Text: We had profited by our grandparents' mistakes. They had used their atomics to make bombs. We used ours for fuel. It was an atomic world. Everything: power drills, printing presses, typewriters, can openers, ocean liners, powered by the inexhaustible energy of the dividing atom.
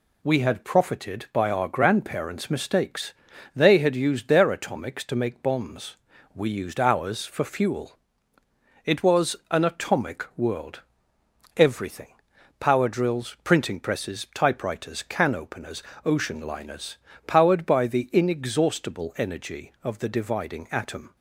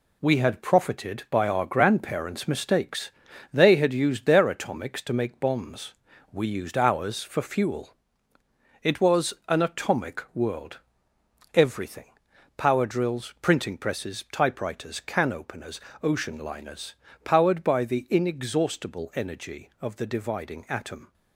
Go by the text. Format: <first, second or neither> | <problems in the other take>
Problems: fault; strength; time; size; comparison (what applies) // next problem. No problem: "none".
first | gets quieter; strong; throughout; 7 dB